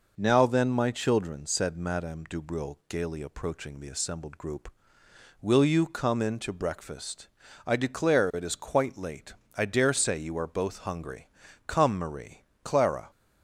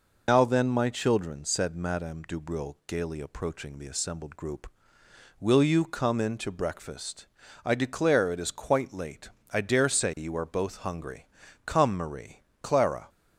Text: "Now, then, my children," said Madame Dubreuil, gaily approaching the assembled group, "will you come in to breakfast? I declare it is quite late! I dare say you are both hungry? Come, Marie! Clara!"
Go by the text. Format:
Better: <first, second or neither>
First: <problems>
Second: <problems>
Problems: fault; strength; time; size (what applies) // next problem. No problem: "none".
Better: first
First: none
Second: loses the start of "Now"; at 0.2 s; 125 ms